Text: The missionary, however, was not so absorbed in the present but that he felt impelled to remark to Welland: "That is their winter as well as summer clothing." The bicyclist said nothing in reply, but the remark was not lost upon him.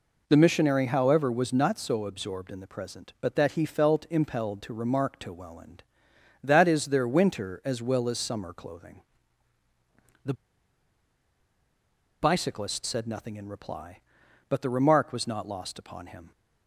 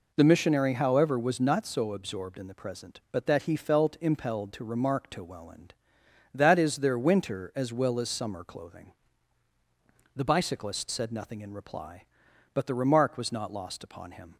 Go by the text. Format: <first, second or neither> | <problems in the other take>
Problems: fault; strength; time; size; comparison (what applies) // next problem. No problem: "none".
second | pauses between "The" and "bicyclist"; strong; at 10.3 s; 1.8 s long